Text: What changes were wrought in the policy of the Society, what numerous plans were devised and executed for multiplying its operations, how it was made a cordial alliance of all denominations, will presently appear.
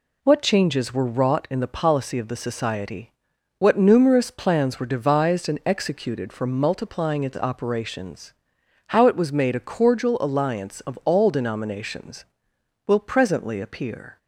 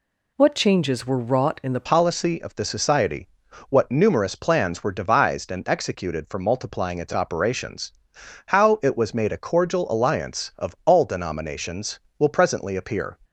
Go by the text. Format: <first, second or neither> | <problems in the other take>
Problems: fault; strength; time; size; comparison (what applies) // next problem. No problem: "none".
first | changes voice at "policy"; from 1.8 s on; 11.3 s long